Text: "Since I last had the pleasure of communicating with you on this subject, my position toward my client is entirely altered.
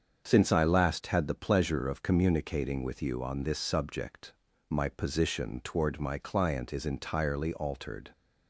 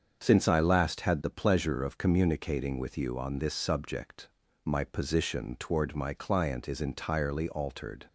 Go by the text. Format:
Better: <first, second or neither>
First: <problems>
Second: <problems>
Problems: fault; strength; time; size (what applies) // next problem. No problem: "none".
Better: neither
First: starts louder than the rest; until 1.3 s; 7 dB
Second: starts louder than the rest; until 1.2 s; 7 dB